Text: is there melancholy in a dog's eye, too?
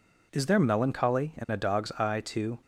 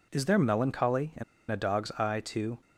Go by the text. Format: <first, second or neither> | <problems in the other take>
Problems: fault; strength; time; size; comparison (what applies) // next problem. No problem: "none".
first | pauses between "in" and "a"; slight; at 1.2 s; 0.27 s long